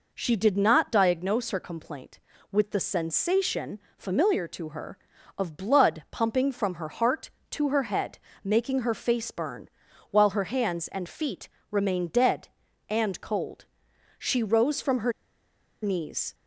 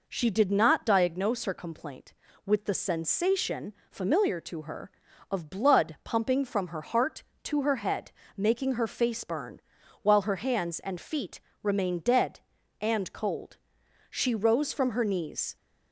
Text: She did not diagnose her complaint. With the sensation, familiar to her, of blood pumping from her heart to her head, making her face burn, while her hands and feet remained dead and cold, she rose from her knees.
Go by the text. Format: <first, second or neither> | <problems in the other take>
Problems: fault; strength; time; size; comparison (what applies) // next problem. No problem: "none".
second | pauses between "feet" and "remained"; slight; at 11.4 s; 0.22 s long; slight in the second // pauses between "her" and "knees"; noticeable; at 15.1 s; 0.70 s long